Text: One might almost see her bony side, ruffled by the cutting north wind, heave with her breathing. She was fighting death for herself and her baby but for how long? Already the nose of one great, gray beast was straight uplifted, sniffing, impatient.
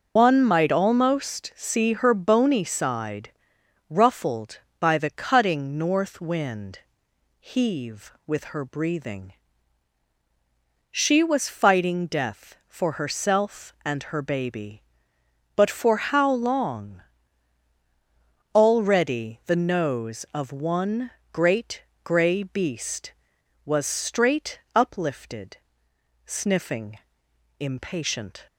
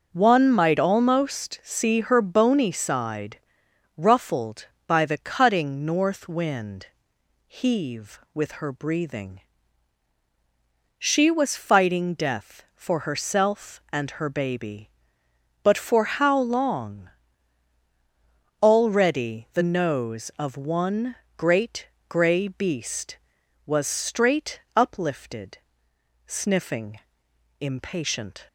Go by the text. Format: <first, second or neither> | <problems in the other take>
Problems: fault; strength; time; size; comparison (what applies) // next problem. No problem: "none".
second | loses the start of "One"; at 0.1 s; 110 ms // pauses between "one" and "great"; slight; at 21.1 s; 0.20 s long; slight in the second // pauses between "straight" and "uplifted"; slight; at 24.6 s; 0.16 s long; slight in the second